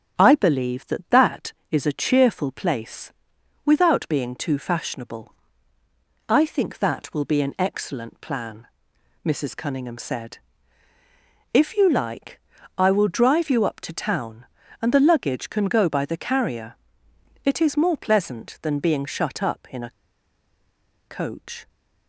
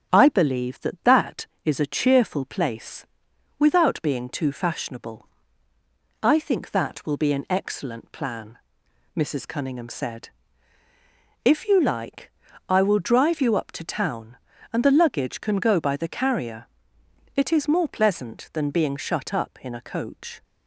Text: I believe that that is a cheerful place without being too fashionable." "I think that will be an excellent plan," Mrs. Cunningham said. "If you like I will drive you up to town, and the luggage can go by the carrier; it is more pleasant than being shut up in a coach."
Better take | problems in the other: second | starts louder than the rest; strong; until 1.2 s; 8 dB; strong in the second // pauses between "place" and "without"; noticeable; at 3.1 s; 0.54 s long; noticeable in the second // pauses between "like" and "I"; at 12.3 s; 0.40 s long; also in the second // pauses between "a" and "coach"; at 19.8 s; 1.1 s long

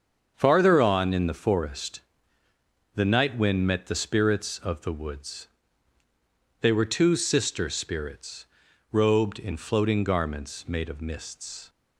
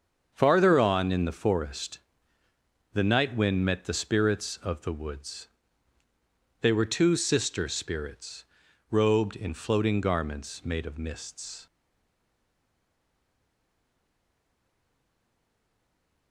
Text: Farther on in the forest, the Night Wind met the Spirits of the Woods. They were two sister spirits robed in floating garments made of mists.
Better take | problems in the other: first | starts louder than the rest; until 1.3 s; 7 dB; also in the first // pauses between "spirits" and "robed"; at 8.4 s; 0.44 s long; also in the first // stays silent after the last word; strong; from 11.6 s on; 4.7 s long

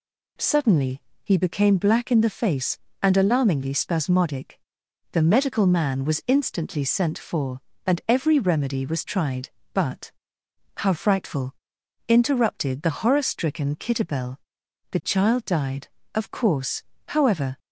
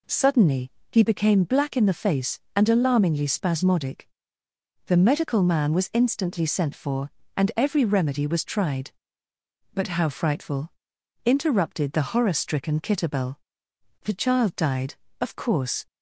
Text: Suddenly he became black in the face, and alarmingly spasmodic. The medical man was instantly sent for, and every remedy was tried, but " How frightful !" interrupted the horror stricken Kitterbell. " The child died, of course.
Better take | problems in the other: second | pauses between "Suddenly" and "he"; slight; at 1.0 s; 0.24 s long; slight in the second // goes on to say "However"; from 17.0 s on; 0.52 s long

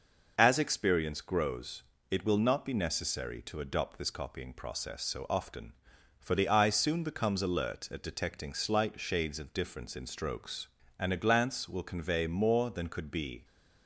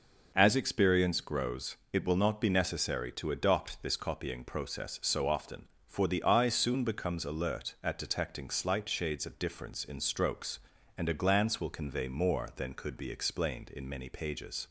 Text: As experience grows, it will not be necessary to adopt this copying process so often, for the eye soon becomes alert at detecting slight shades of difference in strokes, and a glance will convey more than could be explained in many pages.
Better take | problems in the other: second | stops before "explained in many pages"; at 13.4 s

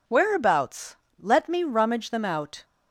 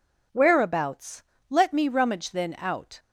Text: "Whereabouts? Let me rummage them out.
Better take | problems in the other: first | says "then" for "them"; at 2.3 s

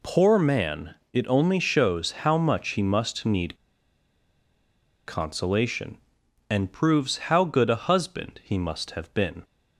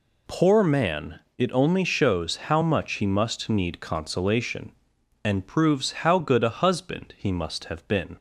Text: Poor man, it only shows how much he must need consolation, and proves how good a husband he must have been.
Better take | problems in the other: second | pauses between "need" and "consolation"; strong; at 3.5 s; 1.5 s long

